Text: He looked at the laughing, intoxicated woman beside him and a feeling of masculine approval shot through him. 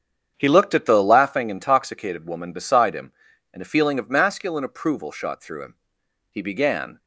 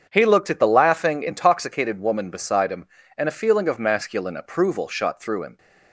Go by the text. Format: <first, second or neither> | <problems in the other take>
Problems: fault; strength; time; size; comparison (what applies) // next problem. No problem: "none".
second | starts louder than the rest; strong; until 1.3 s; 7.5 dB; strong in the second // goes on to say "He began"; noticeable; from 6.3 s on; 0.68 s long